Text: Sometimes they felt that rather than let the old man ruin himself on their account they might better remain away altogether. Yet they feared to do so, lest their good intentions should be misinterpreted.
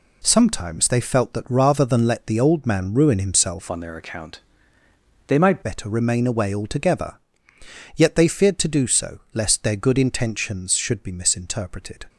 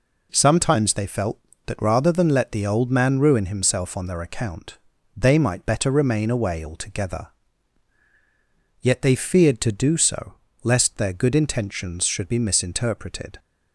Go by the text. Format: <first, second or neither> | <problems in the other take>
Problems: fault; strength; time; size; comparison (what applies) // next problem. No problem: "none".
second | changes voice from "on" to "might"; from 3.6 to 5.6 s; 2.0 s long // pauses between "account" and "they"; noticeable; at 4.3 s; 0.88 s long; also in the second